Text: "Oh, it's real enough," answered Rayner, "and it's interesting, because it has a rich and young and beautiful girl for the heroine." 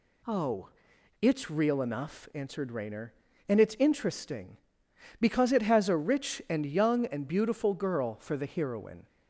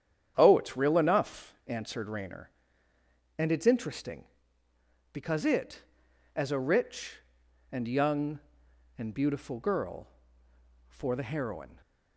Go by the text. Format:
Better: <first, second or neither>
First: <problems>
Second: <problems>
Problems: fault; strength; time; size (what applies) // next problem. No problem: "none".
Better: first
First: none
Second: starts louder than the rest; strong; until 1.3 s; 9 dB // says "as" for "has"; at 6.3 s